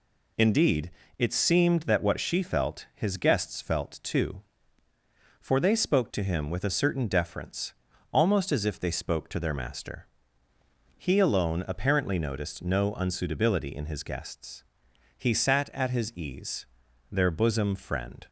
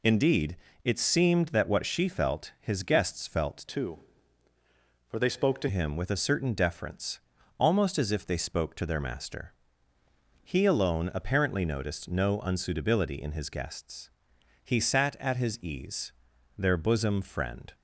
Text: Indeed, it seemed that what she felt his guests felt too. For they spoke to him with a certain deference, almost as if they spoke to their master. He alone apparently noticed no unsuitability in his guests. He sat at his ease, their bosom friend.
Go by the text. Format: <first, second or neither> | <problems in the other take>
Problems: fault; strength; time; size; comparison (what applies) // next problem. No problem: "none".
first | changes voice from "too" to "to"; from 3.6 to 5.6 s; 2.0 s long